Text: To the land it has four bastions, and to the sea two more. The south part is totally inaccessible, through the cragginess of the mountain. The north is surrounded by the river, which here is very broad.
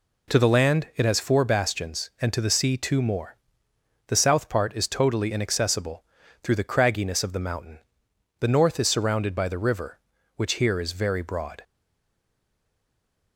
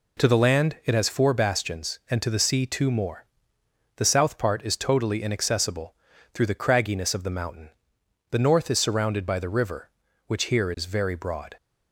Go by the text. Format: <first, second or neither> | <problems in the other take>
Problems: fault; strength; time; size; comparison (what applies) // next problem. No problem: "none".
second | stays silent after the last word; noticeable; from 11.6 s on; 1.7 s long